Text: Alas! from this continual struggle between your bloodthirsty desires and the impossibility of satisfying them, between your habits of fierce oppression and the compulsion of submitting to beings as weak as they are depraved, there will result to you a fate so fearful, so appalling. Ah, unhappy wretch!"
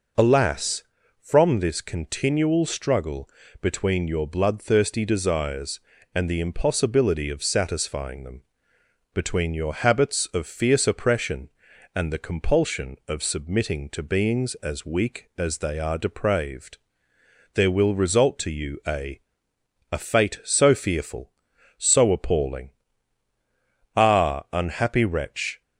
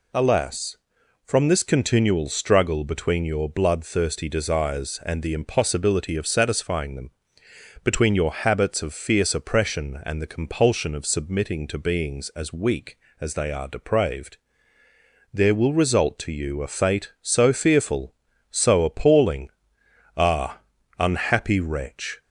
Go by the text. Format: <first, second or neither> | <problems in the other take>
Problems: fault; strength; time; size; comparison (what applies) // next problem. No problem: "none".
second | pauses between "struggle" and "between"; slight; at 3.2 s; 0.34 s long // says "a" twice; at 19.9 s